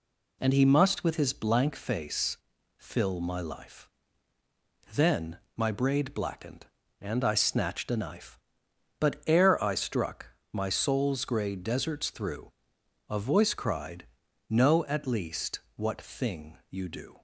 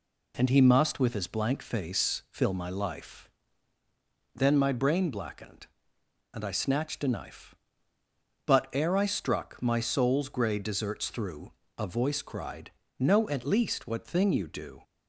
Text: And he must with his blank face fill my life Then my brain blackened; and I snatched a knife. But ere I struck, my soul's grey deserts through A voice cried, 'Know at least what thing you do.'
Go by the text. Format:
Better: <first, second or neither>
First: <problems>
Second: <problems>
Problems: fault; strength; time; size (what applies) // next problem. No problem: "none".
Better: second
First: pauses between "face" and "fill"; at 2.3 s; 0.40 s long // pauses between "life" and "Then"; at 3.8 s; 1.0 s long // pauses between "Then" and "my"; slight; at 5.3 s; 0.18 s long // says "braid" for "brain"; at 5.7 s // pauses between "through" and "A"; noticeable; at 12.5 s; 0.58 s long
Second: pauses between "life" and "Then"; at 3.2 s; 1.0 s long // pauses between "through" and "A"; slight; at 11.5 s; 0.24 s long